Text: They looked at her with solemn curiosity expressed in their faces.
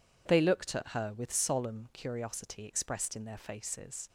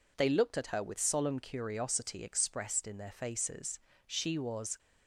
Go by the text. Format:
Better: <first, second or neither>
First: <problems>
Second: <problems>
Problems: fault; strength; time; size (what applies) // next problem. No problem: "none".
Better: first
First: none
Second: goes on to say "She was"; noticeable; from 4.0 s on; 0.72 s long